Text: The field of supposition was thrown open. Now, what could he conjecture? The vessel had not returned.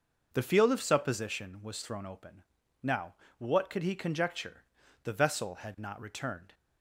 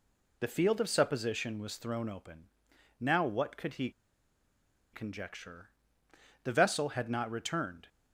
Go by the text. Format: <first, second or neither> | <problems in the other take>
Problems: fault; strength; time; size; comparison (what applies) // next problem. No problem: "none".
first | pauses between "he" and "conjecture"; at 3.8 s; 1.0 s long